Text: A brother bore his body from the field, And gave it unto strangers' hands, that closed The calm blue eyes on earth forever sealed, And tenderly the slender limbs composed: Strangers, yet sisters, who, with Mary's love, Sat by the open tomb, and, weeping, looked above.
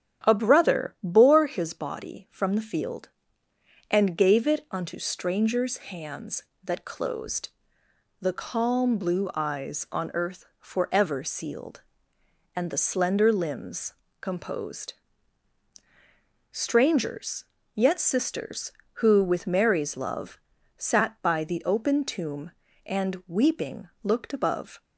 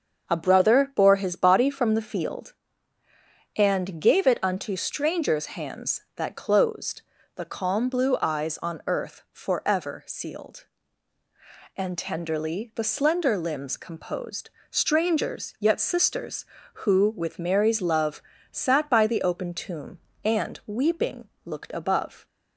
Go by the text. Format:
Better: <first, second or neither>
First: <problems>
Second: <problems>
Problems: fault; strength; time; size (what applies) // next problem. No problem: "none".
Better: second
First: starts louder than the rest; strong; until 1.3 s; 9 dB // pauses between "closed" and "The"; noticeable; at 7.4 s; 0.72 s long // skips "tenderly"; at 12.7 s // pauses between "limbs" and "composed"; slight; at 13.9 s; 0.26 s long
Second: starts louder than the rest; until 1.3 s; 6.5 dB // pauses between "closed" and "The"; slight; at 7.0 s; 0.32 s long